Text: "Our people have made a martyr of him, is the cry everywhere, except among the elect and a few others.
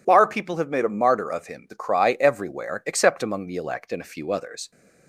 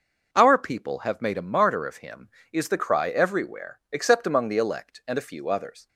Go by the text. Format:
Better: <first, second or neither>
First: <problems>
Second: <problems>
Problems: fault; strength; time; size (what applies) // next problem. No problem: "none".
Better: second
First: skips "is"; at 1.6 s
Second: none